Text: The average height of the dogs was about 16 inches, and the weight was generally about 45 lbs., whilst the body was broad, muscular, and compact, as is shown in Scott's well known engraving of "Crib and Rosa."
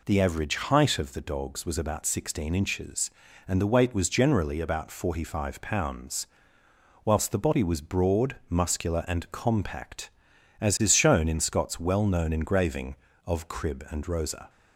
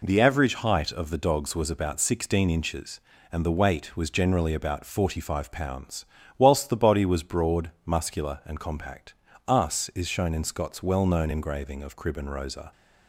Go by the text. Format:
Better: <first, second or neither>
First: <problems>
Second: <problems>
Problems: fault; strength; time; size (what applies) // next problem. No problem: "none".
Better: first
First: none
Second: says "us" for "as"; at 9.4 s